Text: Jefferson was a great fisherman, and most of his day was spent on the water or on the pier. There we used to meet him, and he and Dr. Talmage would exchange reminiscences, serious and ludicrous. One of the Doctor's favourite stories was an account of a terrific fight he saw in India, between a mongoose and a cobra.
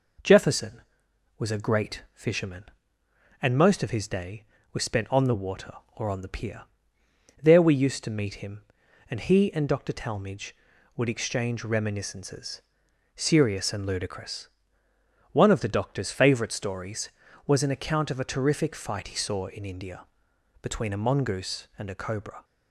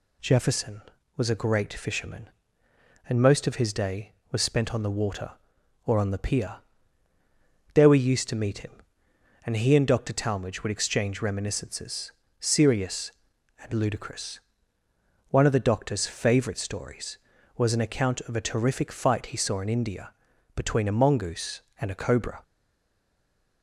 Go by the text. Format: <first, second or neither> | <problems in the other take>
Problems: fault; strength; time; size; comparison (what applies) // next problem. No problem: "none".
first | stays silent after the last word; noticeable; from 22.4 s on; 1.2 s long